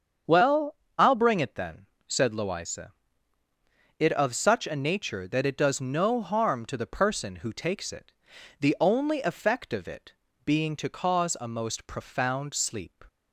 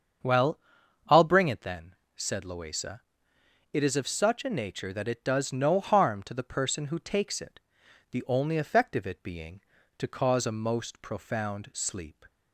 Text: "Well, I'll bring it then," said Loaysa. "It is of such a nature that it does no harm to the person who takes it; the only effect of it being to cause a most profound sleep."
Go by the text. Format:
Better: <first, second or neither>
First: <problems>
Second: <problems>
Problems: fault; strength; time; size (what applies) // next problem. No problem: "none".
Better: second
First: starts louder than the rest; strong; until 1.5 s; 7 dB // skips "is"; at 4.1 s // pauses between "it" and "being"; slight; at 10.1 s; 0.32 s long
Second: starts louder than the rest; until 1.7 s; 7 dB